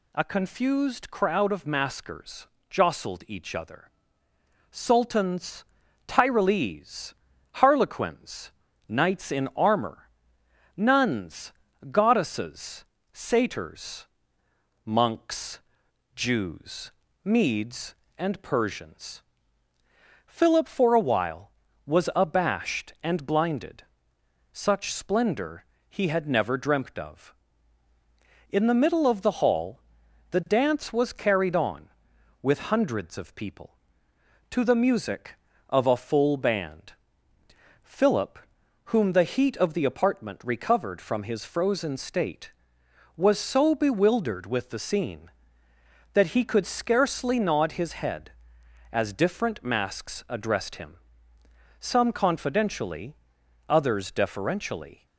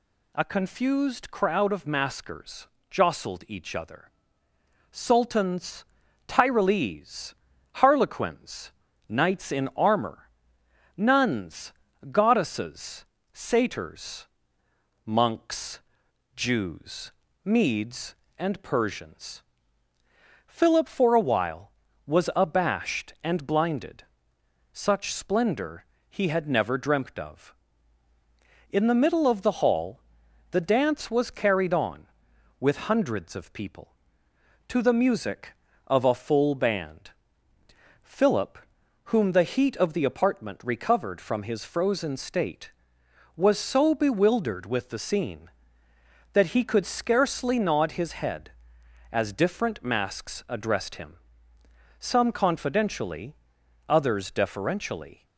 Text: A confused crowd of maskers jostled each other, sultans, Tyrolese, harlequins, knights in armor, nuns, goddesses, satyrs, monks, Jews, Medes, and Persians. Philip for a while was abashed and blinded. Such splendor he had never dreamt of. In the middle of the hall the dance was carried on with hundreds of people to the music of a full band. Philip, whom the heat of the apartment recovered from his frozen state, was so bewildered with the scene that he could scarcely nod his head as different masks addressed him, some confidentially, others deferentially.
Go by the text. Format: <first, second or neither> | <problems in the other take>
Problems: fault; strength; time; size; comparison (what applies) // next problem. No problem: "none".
neither | pauses between "maskers" and "jostled"; slight; the same in both // pauses between "splendor" and "he"; slight; the same in both // pauses between "hall" and "the"; noticeable; the same in both